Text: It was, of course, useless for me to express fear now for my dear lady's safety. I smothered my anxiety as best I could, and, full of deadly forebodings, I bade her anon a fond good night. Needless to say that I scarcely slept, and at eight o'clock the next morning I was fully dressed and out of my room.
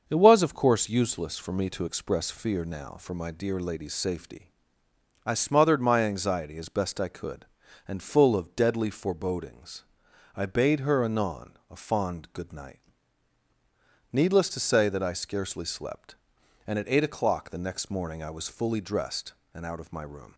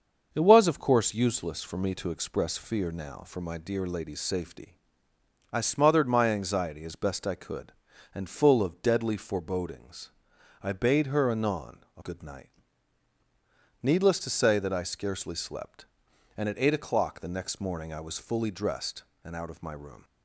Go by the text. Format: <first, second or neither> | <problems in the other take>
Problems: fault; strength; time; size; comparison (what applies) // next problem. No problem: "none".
first | starts louder than the rest; until 1.3 s; 6.5 dB; also in the first // pauses between "anon" and "a"; slight; at 11.7 s; 0.18 s long; slight in the first // skips "fond"; at 12.0 s